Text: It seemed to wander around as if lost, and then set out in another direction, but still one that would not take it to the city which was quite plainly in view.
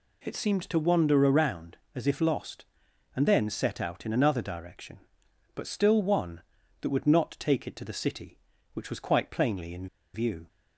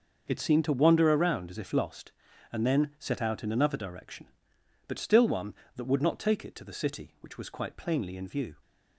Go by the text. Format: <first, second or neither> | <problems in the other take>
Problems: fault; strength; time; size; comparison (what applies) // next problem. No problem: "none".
second | pauses between "in" and "view"; slight; at 9.8 s; 0.27 s long